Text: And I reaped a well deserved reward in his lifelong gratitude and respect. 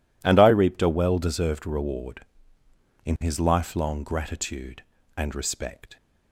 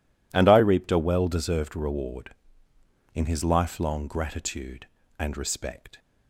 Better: neither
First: none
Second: none

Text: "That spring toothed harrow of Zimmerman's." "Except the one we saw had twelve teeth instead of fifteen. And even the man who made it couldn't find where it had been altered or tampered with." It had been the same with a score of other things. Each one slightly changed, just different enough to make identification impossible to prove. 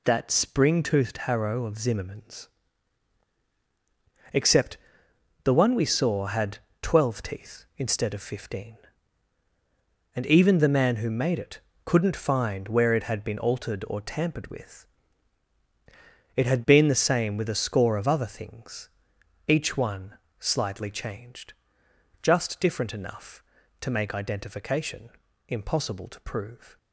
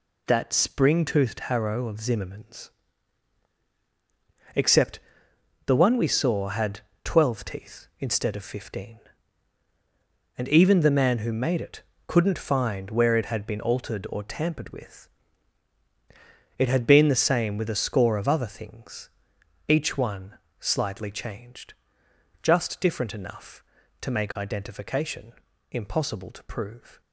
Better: neither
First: pauses between "Except" and "the"; noticeable; at 4.7 s; 0.66 s long // pauses between "had" and "twelve"; slight; at 6.5 s; 0.24 s long // pauses between "it" and "couldn't"; slight; at 11.5 s; 0.26 s long // pauses between "one" and "slightly"; slight; at 20.1 s; 0.22 s long // pauses between "identification" and "impossible"; slight; at 25.1 s; 0.36 s long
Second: pauses between "Except" and "the"; noticeable; at 4.9 s; 0.66 s long // pauses between "had" and "twelve"; slight; at 6.7 s; 0.24 s long // pauses between "it" and "couldn't"; slight; at 11.8 s; 0.26 s long // pauses between "one" and "slightly"; slight; at 20.3 s; 0.22 s long // pauses between "identification" and "impossible"; slight; at 25.3 s; 0.36 s long

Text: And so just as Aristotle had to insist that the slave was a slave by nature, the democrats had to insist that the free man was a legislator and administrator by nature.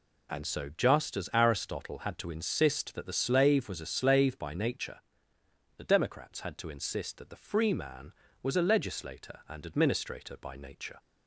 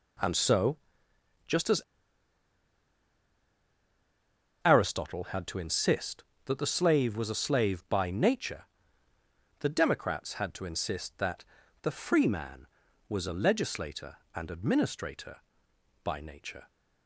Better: first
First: none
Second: pauses between "so" and "just"; noticeable; at 0.7 s; 0.68 s long // pauses between "as" and "Aristotle"; strong; at 1.7 s; 2.8 s long // pauses between "that" and "the"; at 11.4 s; 0.40 s long

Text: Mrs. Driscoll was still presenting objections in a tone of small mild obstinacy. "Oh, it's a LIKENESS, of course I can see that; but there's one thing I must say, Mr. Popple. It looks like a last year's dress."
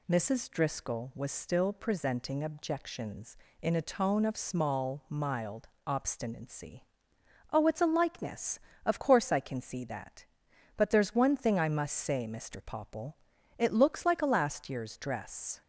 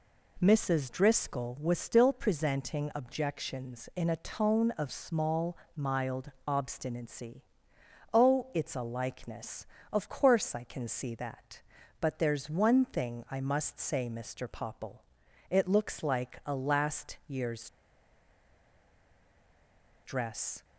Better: first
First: pauses between "mild" and "obstinacy"; slight; at 5.6 s; 0.18 s long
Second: pauses between "small" and "mild"; slight; at 5.5 s; 0.16 s long // pauses between "mild" and "obstinacy"; slight; at 6.2 s; 0.16 s long // pauses between "year's" and "dress"; strong; at 17.6 s; 2.3 s long

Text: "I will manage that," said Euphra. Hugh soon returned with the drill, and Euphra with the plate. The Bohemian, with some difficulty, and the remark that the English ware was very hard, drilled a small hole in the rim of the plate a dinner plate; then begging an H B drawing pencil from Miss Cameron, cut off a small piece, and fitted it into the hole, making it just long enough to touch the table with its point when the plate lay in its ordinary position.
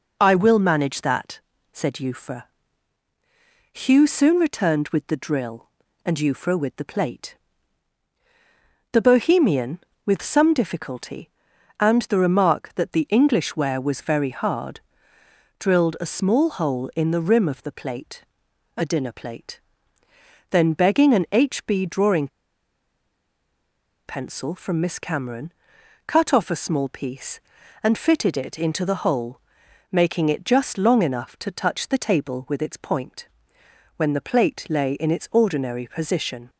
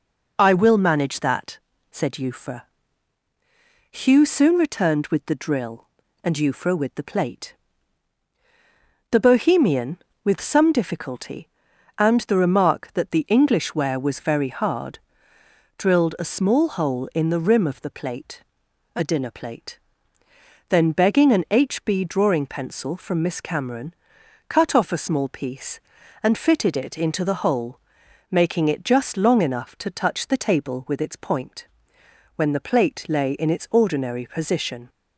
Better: second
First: pauses between "plate" and "a"; noticeable; at 18.2 s; 0.56 s long // pauses between "drawing" and "pencil"; strong; at 22.2 s; 1.7 s long // pauses between "point" and "when"; noticeable; at 33.2 s; 0.68 s long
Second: pauses between "plate" and "a"; noticeable; at 18.4 s; 0.56 s long // pauses between "point" and "when"; noticeable; at 31.6 s; 0.68 s long

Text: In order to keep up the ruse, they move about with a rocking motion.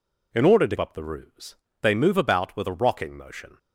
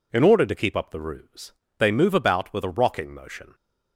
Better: second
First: skips "keep"; at 0.7 s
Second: none

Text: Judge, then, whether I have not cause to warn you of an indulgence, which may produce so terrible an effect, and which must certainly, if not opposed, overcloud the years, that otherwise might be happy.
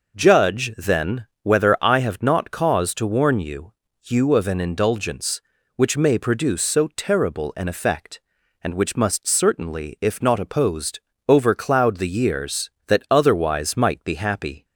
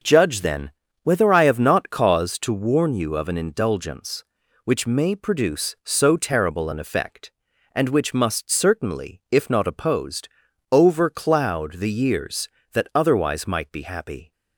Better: second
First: says "you" twice; at 4.0 s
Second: none

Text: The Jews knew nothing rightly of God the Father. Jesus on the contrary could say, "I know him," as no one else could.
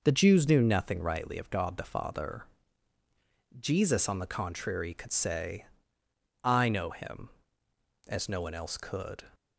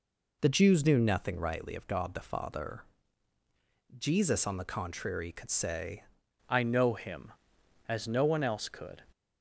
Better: first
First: none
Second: changes voice at "I"; from 6.4 s on; 2.6 s long

